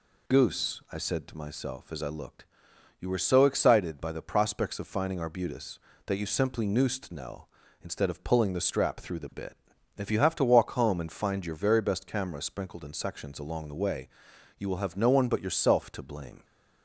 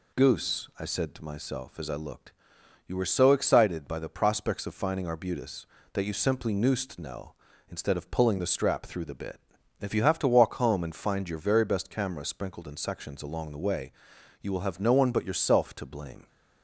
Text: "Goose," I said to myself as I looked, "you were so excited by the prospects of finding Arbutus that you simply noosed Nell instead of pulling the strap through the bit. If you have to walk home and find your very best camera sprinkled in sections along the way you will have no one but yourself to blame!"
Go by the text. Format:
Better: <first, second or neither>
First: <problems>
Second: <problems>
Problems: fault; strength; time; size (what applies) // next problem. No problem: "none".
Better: neither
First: pauses between "way" and "you"; noticeable; at 14.0 s; 0.48 s long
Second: pauses between "way" and "you"; noticeable; at 13.9 s; 0.48 s long